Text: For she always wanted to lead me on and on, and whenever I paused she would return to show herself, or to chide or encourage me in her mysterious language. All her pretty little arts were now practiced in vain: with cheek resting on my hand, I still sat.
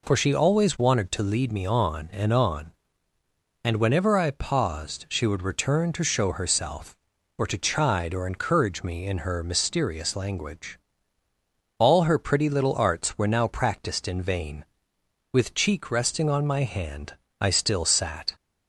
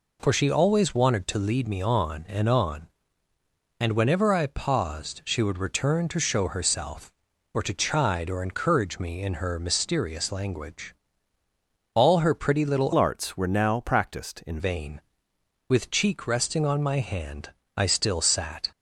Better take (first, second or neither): first